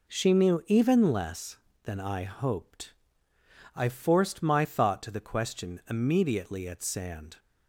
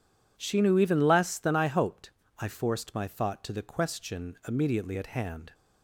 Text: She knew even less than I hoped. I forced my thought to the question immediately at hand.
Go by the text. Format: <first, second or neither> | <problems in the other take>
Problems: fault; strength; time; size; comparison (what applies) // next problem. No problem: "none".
second | says "sand" for "hand"; at 6.8 s